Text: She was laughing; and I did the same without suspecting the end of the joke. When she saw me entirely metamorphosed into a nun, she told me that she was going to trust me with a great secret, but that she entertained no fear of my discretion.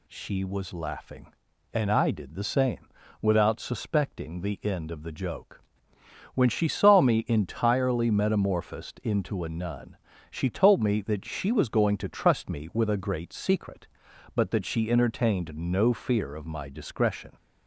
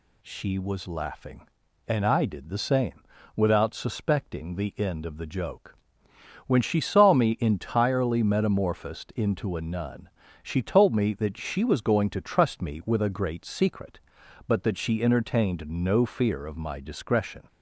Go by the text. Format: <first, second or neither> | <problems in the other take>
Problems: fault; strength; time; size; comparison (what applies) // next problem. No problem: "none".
neither | pauses between "same" and "without"; slight; the same in both